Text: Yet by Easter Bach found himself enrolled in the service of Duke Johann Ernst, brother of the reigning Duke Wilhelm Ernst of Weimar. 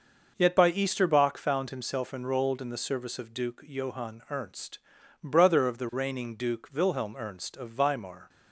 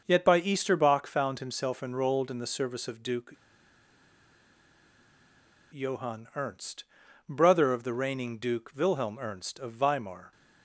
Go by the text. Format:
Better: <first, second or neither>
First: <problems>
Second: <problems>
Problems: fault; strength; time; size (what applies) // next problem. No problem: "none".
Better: first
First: none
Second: starts louder than the rest; noticeable; until 1.0 s; 6 dB // pauses between "Duke" and "Johann"; strong; at 3.3 s; 2.4 s long